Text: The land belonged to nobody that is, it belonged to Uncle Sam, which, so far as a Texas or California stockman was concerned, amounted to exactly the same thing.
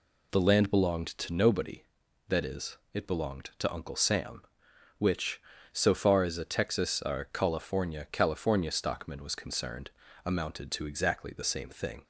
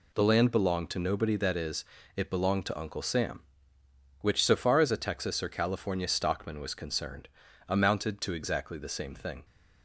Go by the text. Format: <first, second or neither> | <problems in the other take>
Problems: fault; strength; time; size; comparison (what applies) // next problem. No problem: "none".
second | says "California" twice; at 8.1 s